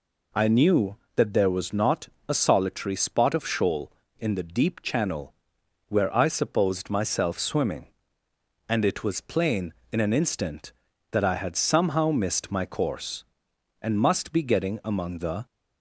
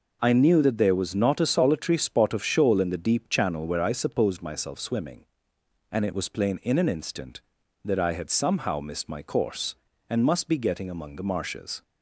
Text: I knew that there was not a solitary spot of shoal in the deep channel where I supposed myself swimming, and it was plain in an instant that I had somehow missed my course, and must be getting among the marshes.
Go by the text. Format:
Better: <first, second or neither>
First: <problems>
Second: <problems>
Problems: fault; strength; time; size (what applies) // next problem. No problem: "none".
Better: second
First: pauses between "not" and "a"; slight; at 2.0 s; 0.19 s long // pauses between "channel" and "where"; noticeable; at 5.3 s; 0.56 s long // stops before "marshes"; at 15.4 s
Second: none